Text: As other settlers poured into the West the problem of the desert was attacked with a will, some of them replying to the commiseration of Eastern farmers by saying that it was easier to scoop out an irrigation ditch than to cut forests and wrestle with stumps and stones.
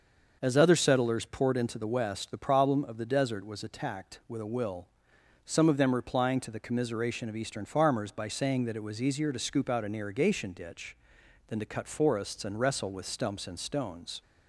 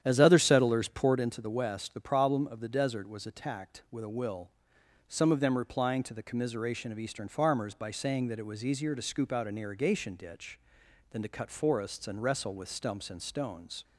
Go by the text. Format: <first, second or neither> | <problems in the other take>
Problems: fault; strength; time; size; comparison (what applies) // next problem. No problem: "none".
first | starts louder than the rest; strong; until 1.2 s; 9.5 dB